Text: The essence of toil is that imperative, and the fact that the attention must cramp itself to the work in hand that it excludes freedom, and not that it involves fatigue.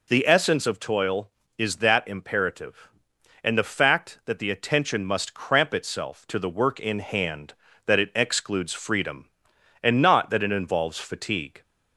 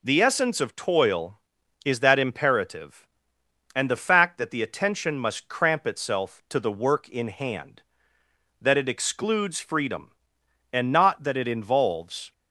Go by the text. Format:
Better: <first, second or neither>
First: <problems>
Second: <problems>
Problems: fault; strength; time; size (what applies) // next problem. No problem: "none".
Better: first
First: none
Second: stops before "fatigue"; at 12.3 s